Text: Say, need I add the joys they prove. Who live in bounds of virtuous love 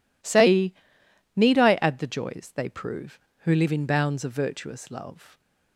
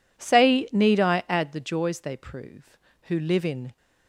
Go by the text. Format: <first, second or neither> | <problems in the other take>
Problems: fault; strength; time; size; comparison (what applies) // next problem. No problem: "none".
first | stops before "bounds of virtuous love"; at 3.7 s